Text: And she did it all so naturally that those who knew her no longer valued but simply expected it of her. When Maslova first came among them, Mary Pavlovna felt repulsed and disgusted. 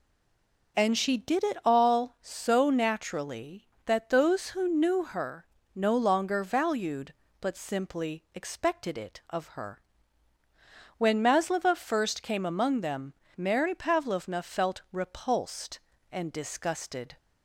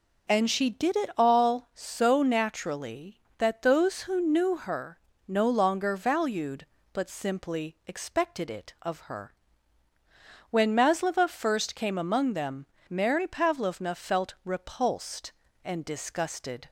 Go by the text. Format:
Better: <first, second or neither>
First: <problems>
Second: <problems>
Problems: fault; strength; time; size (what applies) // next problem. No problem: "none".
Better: second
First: stays silent before the first word; slight; until 0.7 s; 0.7 s long // pauses between "her" and "no"; slight; at 5.4 s; 0.28 s long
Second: pauses between "her" and "no"; slight; at 4.9 s; 0.28 s long